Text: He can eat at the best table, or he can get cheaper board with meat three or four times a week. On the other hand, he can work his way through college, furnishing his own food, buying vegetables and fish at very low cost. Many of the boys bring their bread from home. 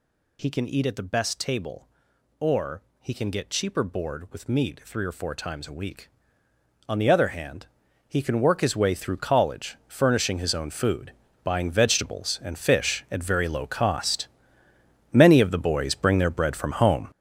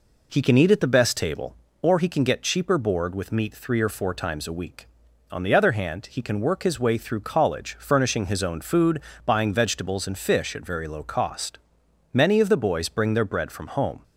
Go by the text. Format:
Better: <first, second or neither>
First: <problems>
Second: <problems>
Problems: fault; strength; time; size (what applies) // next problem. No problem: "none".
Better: second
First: gets louder; strong; throughout; 9.5 dB // pauses between "or" and "he"; slight; at 2.8 s; 0.18 s long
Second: none